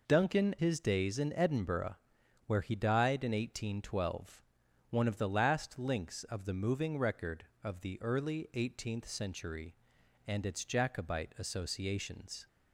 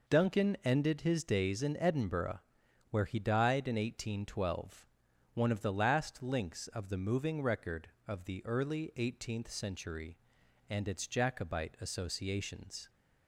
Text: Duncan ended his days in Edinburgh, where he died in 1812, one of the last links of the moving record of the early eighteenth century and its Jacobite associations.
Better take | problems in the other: second | skips "ended"; at 0.5 s

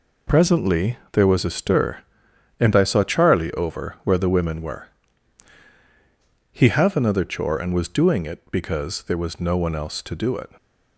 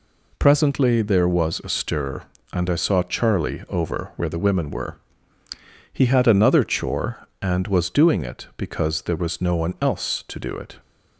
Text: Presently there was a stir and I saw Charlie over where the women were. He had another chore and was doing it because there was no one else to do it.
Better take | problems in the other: second | says "have" for "had"; at 6.6 s

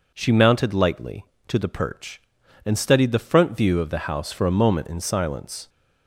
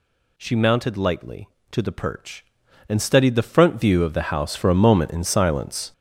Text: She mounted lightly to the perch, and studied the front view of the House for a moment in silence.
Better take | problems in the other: first | gets louder; strong; throughout; 7 dB

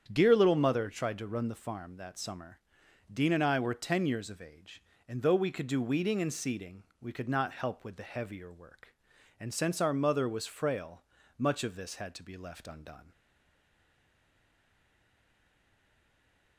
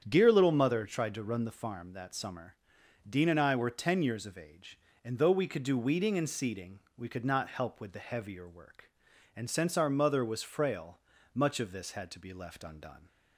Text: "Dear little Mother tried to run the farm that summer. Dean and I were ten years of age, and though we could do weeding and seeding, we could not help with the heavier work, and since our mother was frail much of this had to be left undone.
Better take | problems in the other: second | starts louder than the rest; strong; until 1.1 s; 8.5 dB; strong in the second // pauses between "frail" and "much"; slight; at 11.0 s; 0.34 s long; slight in the second // stays silent after the last word; strong; from 13.1 s on; 3.4 s long

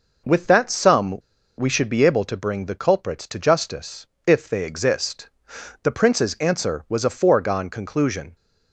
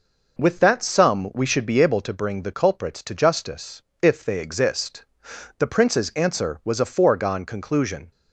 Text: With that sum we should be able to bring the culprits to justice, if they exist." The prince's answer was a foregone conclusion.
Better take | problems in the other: second | pauses between "sum" and "we"; at 1.1 s; 0.40 s long

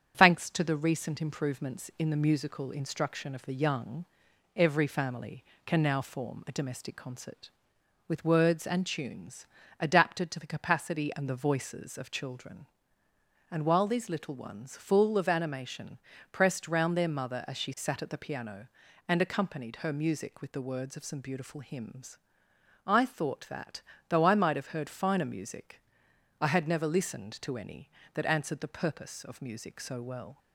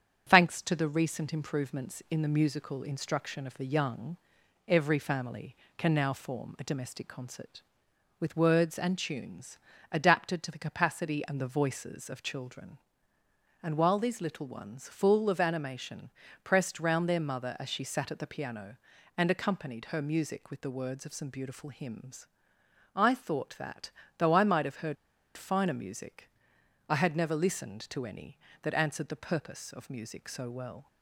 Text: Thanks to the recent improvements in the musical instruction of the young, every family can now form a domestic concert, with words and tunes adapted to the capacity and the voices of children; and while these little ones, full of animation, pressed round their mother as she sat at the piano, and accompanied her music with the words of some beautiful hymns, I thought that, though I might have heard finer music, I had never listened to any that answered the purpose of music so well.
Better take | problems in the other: first | starts louder than the rest; strong; until 1.3 s; 8 dB; strong in the first // pauses between "tunes" and "adapted"; slight; at 9.5 s; 0.32 s long; slight in the first // pauses between "heard" and "finer"; at 24.9 s; 0.41 s long

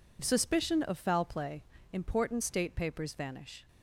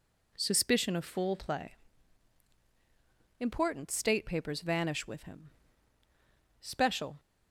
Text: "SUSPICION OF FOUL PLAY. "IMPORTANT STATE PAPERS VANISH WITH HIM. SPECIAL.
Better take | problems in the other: second | stops before "WITH HIM SPECIAL"; at 3.6 s

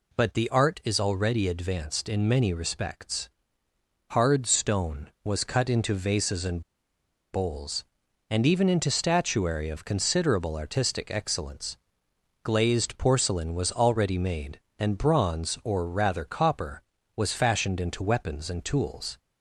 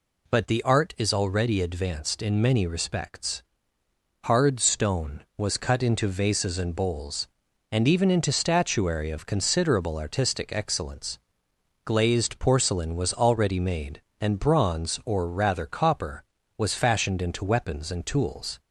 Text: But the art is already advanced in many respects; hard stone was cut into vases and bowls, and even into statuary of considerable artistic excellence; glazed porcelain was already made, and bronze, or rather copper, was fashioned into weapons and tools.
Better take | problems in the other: second | pauses between "and" and "bowls"; noticeable; at 6.6 s; 0.73 s long

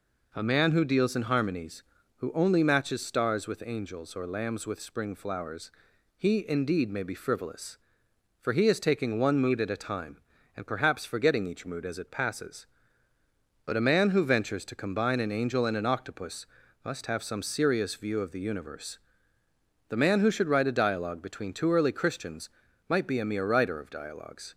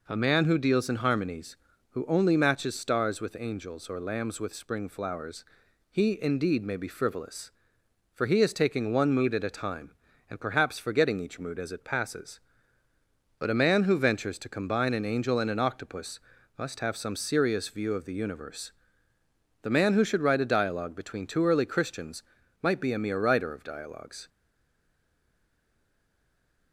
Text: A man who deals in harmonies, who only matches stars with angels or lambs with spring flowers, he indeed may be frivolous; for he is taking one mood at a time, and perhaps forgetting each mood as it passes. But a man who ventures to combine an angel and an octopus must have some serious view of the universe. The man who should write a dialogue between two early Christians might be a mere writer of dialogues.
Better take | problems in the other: first | pauses between "octopus" and "must"; slight; at 16.2 s; 0.36 s long; slight in the first // pauses between "Christians" and "might"; at 22.2 s; 0.40 s long; also in the first // stays silent after the last word; from 24.2 s on; 2.5 s long

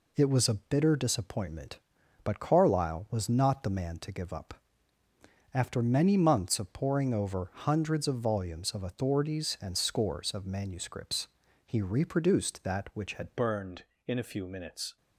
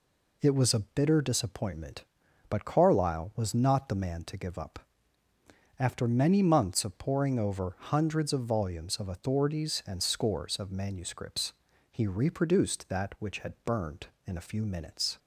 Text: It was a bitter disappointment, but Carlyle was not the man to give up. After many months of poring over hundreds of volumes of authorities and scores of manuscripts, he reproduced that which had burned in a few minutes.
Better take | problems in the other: second | changes voice at "burned"; from 13.3 s on; 1.6 s long

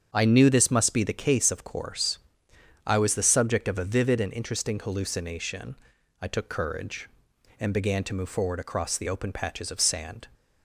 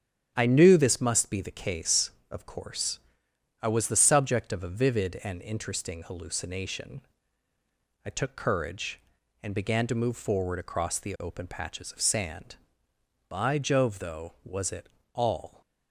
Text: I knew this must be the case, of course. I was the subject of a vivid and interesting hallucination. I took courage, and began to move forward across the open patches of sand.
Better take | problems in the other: first | starts louder than the rest; strong; until 1.3 s; 9 dB; strong in the first // goes on to say "By Jove though was it all"; strong; from 13.2 s on; 2.3 s long

